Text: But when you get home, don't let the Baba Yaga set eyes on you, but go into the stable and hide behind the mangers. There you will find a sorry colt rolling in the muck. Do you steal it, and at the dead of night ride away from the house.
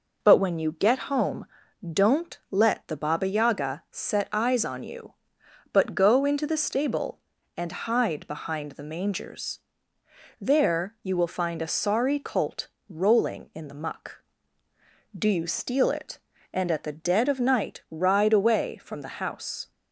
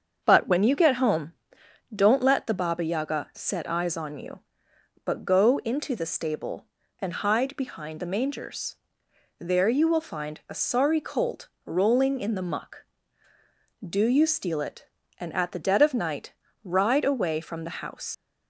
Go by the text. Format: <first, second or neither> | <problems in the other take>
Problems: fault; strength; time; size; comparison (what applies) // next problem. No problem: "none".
first | starts louder than the rest; until 1.2 s; 7 dB // pauses between "colt" and "rolling"; slight; at 11.4 s; 0.16 s long; slight in the first // pauses between "night" and "ride"; slight; at 16.3 s; 0.30 s long // leaves "house" unfinished; at 18.1 s; 75 ms